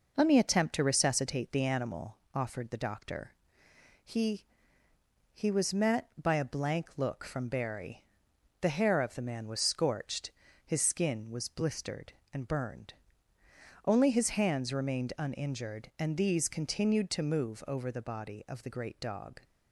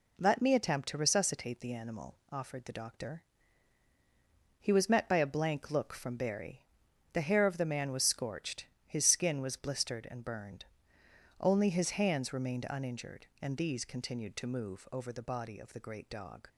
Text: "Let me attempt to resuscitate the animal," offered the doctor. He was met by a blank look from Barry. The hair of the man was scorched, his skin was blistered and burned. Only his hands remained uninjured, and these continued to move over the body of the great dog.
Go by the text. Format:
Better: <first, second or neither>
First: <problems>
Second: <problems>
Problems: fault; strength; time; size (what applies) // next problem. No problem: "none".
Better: second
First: says "He" twice; at 5.3 s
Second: none